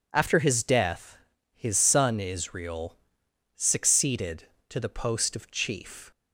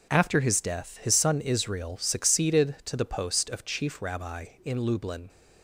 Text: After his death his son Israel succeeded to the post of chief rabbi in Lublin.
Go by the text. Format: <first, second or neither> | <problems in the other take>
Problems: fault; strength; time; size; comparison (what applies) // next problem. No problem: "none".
second | pauses between "death" and "his"; slight; at 1.1 s; 0.36 s long // pauses between "Israel" and "succeeded"; noticeable; at 2.9 s; 0.58 s long // stops before "rabbi in Lublin"; at 6.1 s